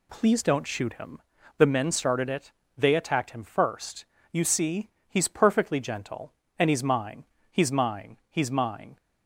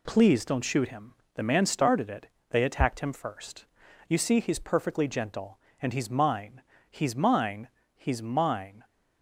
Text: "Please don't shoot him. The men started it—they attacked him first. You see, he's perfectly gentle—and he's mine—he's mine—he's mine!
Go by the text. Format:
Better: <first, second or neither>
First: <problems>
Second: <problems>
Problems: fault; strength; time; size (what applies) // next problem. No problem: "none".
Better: first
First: none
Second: says "man" for "men"; at 1.4 s